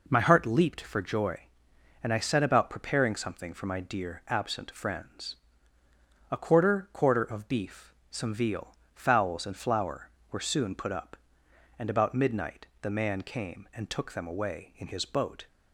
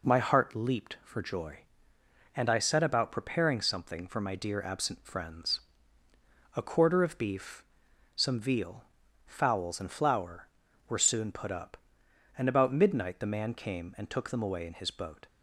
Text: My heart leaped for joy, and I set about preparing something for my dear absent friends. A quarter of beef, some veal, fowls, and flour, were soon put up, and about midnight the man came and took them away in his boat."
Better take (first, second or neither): second